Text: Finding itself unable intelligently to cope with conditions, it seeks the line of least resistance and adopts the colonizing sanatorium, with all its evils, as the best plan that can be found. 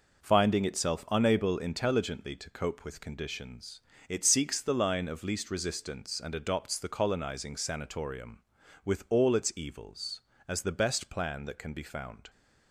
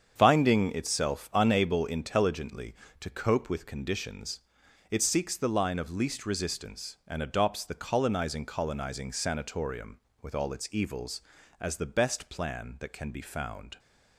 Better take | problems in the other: first | starts louder than the rest; strong; until 1.2 s; 7.5 dB // says "colonizing" twice; at 8.4 s

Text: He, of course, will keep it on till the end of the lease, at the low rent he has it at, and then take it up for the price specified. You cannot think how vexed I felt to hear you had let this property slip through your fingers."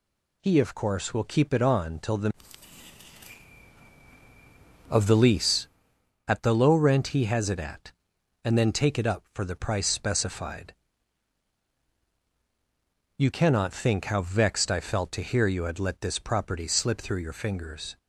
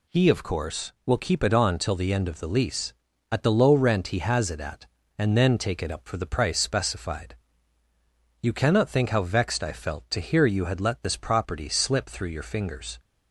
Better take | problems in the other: second | skips "end"; at 3.6 s

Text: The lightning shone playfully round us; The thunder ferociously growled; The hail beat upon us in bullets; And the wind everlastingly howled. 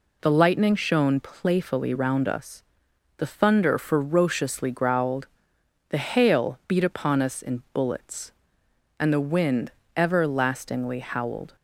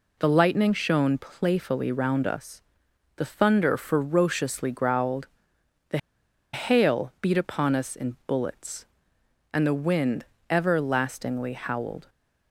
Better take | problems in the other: first | pauses between "The" and "hail"; noticeable; at 5.9 s; 0.55 s long // pauses between "wind" and "everlastingly"; slight; at 10.2 s; 0.26 s long; slight in the first

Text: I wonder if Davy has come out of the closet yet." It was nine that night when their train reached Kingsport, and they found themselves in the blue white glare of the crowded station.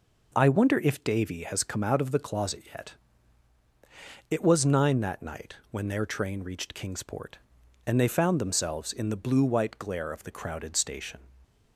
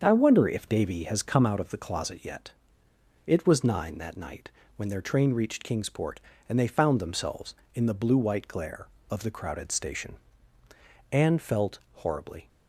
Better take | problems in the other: first | starts louder than the rest; until 1.0 s; 6.5 dB // pauses between "night" and "when"; slight; at 4.4 s; 0.26 s long // goes on to say "Anne felt horribly"; from 11.1 s on; 1.3 s long

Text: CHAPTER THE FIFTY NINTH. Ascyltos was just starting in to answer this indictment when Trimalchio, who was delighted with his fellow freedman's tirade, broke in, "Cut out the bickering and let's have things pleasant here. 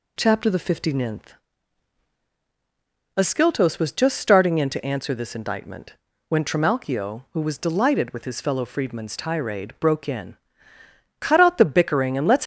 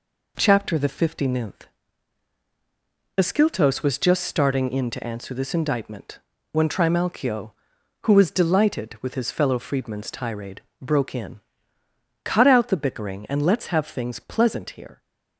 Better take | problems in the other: second | pauses between "indictment" and "when"; at 5.9 s; 0.38 s long; slight in the second // stops before "have things pleasant here"; at 12.4 s

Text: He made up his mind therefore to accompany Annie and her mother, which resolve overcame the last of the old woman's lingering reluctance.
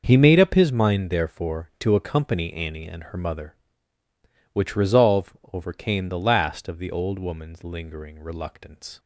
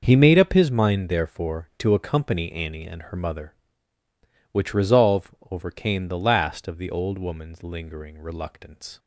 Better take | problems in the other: neither | starts louder than the rest; noticeable; the same in both // pauses between "resolve" and "overcame"; slight; the same in both

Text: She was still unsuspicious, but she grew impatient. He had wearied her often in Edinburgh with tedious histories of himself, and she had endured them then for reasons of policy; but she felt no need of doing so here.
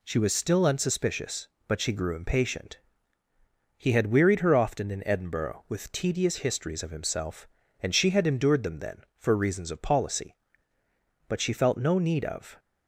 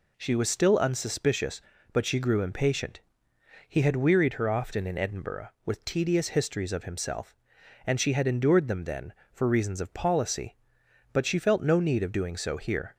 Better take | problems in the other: second | stops before "doing so here"; at 12.5 s

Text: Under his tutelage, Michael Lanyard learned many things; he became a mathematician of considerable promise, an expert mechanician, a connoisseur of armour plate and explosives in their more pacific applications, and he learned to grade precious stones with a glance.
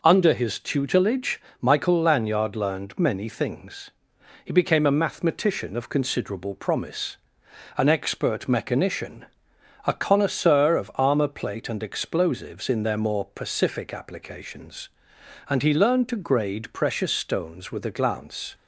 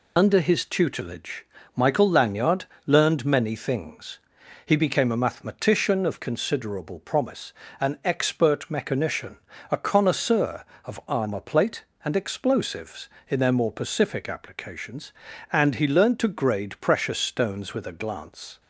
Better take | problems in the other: first | loses the start of "Under"; at 0.1 s; 50 ms // pauses between "Lanyard" and "learned"; slight; at 2.6 s; 0.22 s long

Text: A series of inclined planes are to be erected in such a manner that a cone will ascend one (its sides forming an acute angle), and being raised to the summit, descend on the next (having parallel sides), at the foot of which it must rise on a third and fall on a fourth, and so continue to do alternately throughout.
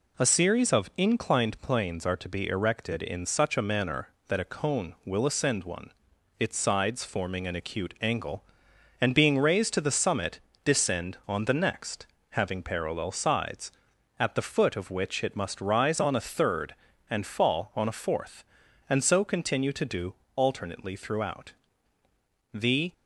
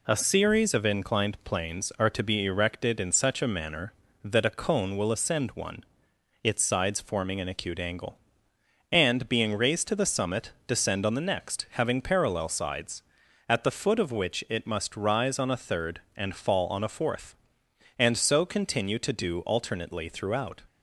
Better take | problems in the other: second | pauses between "do" and "alternately"; slight; at 20.1 s; 0.22 s long // goes on to say "The"; slight; from 22.5 s on; 0.40 s long

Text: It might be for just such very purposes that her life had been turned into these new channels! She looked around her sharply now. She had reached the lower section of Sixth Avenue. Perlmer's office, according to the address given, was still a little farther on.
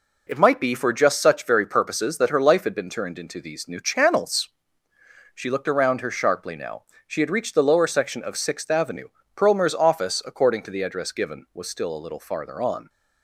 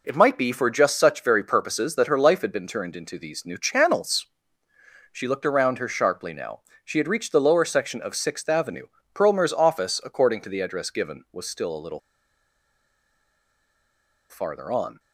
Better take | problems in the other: first | pauses between "little" and "farther"; strong; at 11.9 s; 2.3 s long

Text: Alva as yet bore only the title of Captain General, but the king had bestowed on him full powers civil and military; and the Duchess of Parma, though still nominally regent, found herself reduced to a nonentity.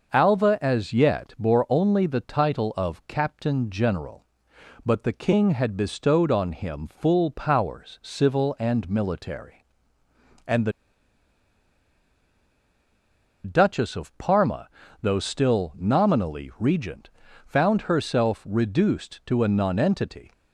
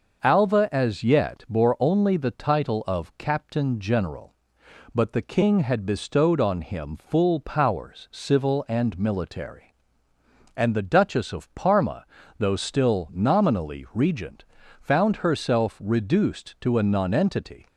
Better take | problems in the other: second | starts louder than the rest; noticeable; until 1.1 s; 6 dB; noticeable in the second // pauses between "the" and "Duchess"; strong; at 10.7 s; 2.7 s long

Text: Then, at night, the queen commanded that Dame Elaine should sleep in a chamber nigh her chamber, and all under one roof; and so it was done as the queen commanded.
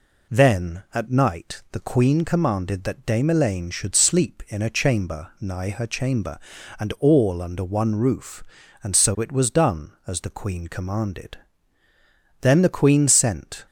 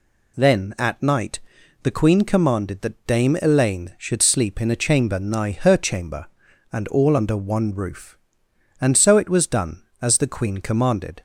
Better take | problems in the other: second | goes on to say "Then the queen sent"; noticeable; from 12.3 s on; 1.2 s long

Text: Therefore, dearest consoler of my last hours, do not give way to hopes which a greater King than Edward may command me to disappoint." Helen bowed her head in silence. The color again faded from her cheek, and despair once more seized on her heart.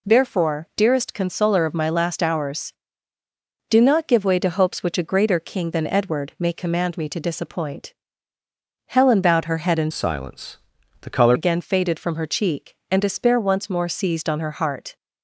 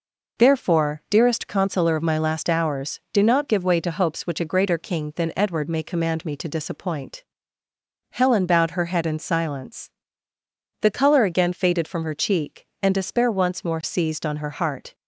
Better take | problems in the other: second | changes voice from "silence" to "color"; from 9.9 to 11.3 s; 1.4 s long

